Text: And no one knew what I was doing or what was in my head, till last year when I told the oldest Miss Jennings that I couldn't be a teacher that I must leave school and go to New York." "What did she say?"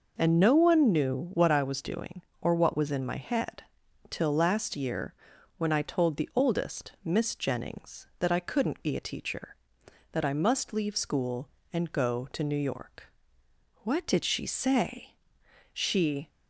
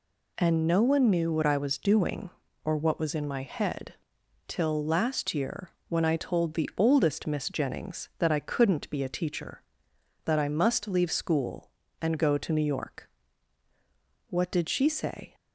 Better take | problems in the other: second | pauses between "year" and "when"; at 5.1 s; 0.44 s long; slight in the second // goes on to say "She"; from 15.7 s on; 0.56 s long

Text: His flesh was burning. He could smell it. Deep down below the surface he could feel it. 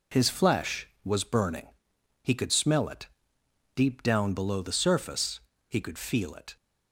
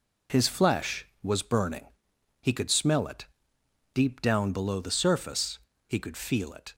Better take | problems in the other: neither | pauses between "surface" and "he"; slight; the same in both

